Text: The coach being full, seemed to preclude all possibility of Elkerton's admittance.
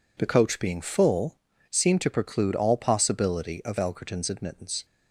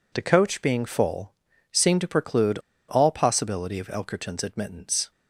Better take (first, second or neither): first